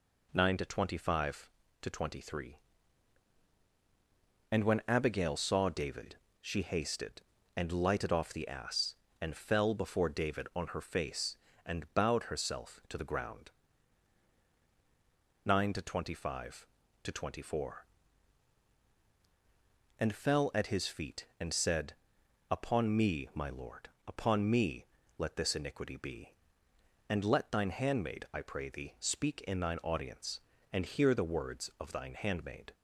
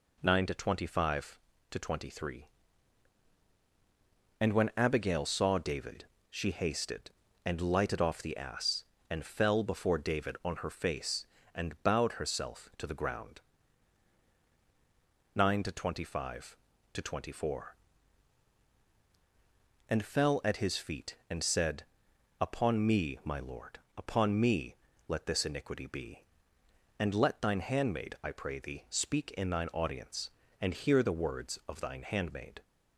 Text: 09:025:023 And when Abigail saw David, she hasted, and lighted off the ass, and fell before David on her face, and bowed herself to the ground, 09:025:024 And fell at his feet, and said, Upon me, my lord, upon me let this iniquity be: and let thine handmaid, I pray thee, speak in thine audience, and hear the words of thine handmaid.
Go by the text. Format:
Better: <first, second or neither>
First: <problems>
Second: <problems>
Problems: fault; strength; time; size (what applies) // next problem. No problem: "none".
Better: neither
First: pauses between "me" and "let"; slight; at 24.8 s; 0.34 s long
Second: pauses between "me" and "let"; slight; at 24.7 s; 0.34 s long